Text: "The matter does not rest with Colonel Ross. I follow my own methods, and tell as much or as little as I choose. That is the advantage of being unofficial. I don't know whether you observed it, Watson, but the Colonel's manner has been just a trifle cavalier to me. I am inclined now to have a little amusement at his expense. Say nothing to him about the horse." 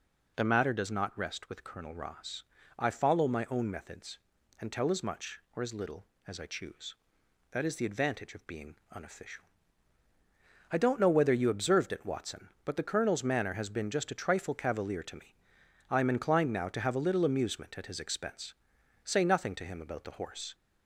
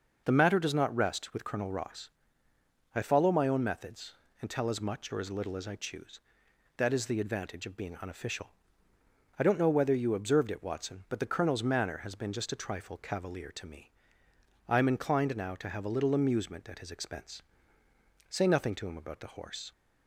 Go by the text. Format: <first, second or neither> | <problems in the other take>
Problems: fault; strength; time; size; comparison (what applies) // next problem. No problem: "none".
neither | none